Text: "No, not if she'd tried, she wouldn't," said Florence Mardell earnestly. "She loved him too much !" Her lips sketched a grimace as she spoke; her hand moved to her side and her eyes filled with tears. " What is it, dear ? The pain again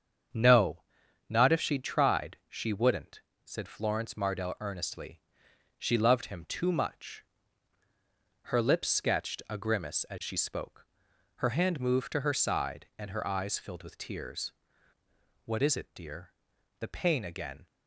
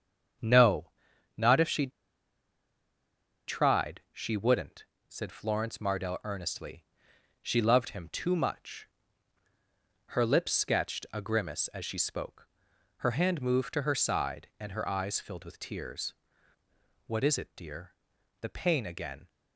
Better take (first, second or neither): first